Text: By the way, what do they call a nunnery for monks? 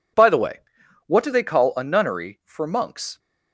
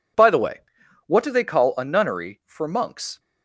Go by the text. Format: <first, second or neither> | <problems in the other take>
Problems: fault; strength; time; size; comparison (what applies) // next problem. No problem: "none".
neither | none